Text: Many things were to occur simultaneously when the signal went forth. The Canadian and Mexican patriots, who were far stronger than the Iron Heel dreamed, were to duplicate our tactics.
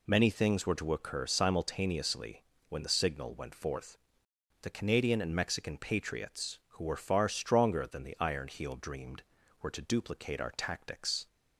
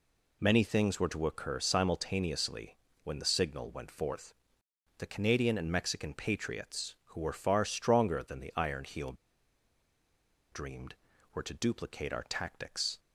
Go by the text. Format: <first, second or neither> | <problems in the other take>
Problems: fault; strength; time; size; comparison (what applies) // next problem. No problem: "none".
first | pauses between "simultaneously" and "when"; slight; at 2.7 s; 0.30 s long; slight in the first // pauses between "Heel" and "dreamed"; strong; at 9.1 s; 1.3 s long